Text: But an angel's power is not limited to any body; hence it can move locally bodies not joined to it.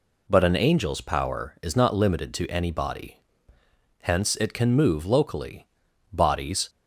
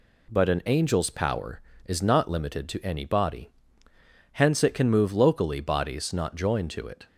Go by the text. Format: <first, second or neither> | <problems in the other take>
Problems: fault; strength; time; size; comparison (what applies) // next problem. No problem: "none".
second | pauses between "locally" and "bodies"; at 5.6 s; 0.44 s long // stops before "not joined to it"; at 6.6 s